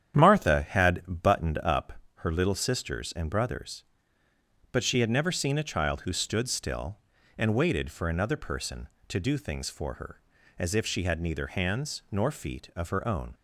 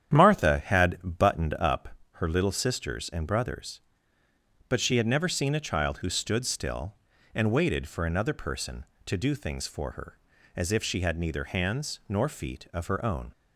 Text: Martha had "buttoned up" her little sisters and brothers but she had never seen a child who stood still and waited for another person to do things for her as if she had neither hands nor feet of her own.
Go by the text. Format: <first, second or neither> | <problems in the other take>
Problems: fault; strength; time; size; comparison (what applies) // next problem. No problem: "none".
neither | starts louder than the rest; strong; the same in both // pauses between "up" and "her"; slight; the same in both